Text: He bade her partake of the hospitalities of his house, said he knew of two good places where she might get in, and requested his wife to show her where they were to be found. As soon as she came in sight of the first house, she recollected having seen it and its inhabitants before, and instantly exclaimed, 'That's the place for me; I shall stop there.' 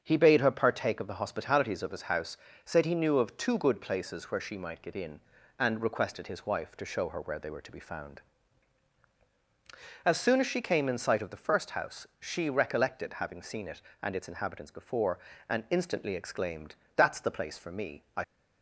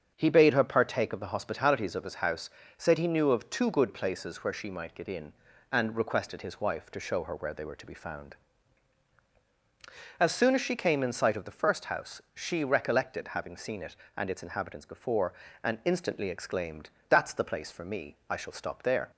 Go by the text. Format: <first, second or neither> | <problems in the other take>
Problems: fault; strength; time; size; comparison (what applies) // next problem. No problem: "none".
second | starts louder than the rest; strong; until 1.0 s; 7 dB; strong in the second // stops before "shall stop there"; at 18.2 s